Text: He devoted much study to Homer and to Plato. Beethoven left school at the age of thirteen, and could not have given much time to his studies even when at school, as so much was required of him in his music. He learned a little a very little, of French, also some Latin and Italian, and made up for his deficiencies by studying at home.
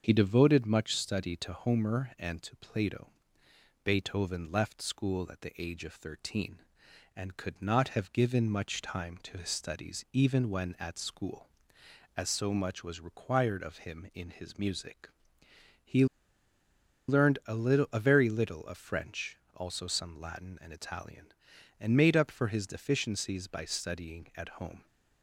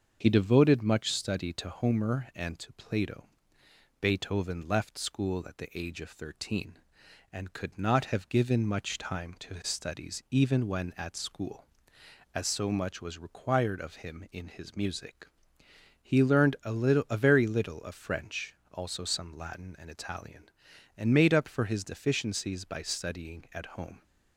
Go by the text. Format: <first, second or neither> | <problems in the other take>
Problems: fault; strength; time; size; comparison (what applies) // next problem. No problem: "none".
second | starts louder than the rest; until 1.0 s; 7 dB; also in the second // pauses between "He" and "learned"; at 16.0 s; 1.0 s long